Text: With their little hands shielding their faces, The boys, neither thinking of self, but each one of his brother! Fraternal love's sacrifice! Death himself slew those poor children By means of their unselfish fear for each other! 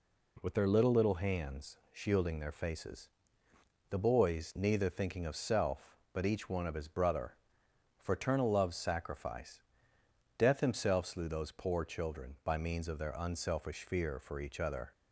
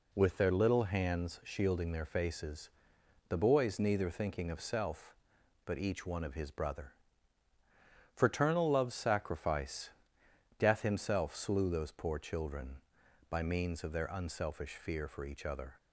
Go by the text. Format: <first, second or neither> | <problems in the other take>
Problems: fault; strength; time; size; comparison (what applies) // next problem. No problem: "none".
second | says "little" twice; at 0.9 s